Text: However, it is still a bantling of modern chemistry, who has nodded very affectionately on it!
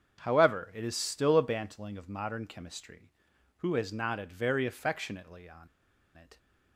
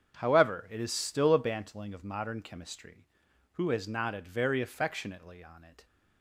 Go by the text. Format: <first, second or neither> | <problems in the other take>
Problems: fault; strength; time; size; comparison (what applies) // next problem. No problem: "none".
second | starts louder than the rest; strong; until 1.2 s; 7.5 dB; strong in the second // pauses between "on" and "it"; noticeable; at 5.6 s; 0.48 s long